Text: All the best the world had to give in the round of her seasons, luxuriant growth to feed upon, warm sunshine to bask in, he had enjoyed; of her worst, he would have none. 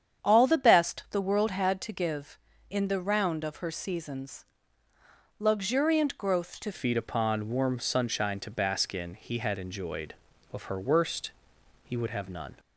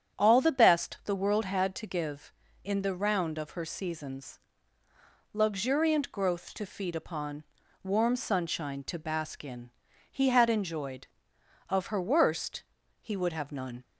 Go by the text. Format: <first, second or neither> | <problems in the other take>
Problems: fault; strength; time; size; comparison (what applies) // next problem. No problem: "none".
second | starts louder than the rest; strong; until 1.3 s; 8.5 dB; strong in the second // changes voice at "feed"; from 6.7 s on; 5.8 s long